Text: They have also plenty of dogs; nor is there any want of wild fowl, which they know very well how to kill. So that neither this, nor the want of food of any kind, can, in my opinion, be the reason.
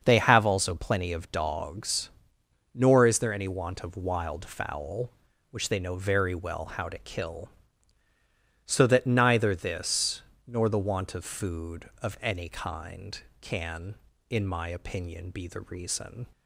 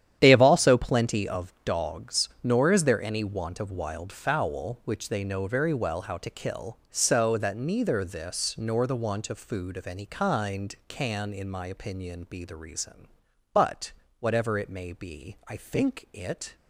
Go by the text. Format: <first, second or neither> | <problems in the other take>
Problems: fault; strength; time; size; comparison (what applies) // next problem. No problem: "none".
first | starts louder than the rest; strong; until 1.2 s; 10.5 dB; also in the first // goes on to say "But whatever it may be I think it"; strong; from 13.5 s on; 3.0 s long